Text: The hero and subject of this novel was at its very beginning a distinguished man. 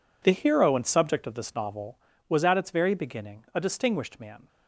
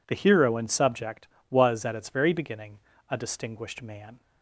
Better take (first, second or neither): first